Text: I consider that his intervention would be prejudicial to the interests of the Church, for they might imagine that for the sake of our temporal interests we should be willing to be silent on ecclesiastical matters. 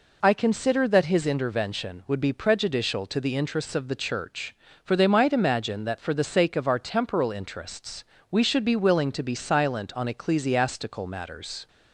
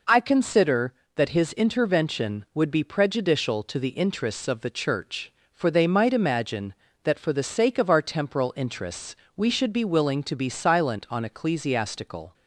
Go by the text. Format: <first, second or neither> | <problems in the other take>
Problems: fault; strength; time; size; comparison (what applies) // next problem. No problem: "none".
first | pauses between "interests" and "we"; slight; at 9.1 s; 0.20 s long; slight in the first // stops before "matters"; at 12.3 s